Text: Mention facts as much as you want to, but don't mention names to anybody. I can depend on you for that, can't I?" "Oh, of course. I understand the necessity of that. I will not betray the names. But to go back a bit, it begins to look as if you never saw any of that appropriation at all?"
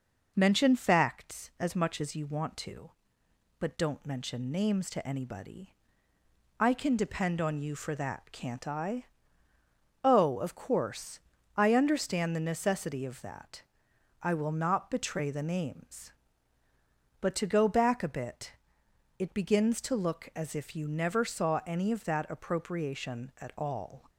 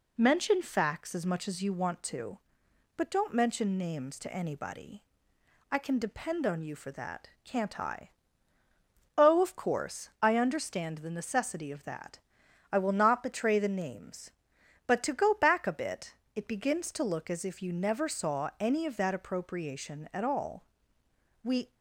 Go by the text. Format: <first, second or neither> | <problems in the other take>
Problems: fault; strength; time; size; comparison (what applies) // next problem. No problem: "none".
first | goes on to say "We"; slight; from 21.4 s on; 0.32 s long